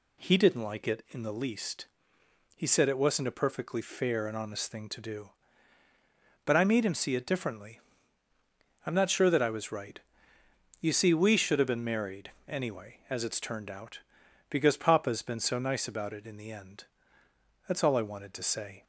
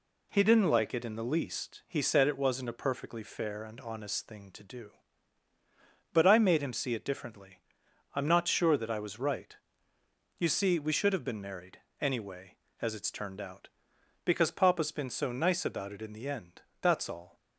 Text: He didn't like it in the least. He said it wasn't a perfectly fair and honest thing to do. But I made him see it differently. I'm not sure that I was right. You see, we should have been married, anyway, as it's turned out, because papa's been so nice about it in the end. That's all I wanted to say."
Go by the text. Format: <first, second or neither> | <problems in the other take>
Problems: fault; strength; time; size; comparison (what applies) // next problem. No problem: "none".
first | stops before "I wanted to say"; at 17.3 s